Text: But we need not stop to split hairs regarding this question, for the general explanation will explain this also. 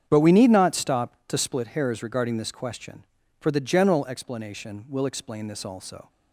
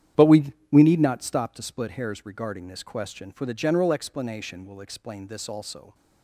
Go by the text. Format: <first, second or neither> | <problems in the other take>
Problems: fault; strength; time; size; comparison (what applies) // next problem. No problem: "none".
first | starts louder than the rest; strong; until 1.3 s; 10 dB; strong in the first // says "we" twice; at 0.7 s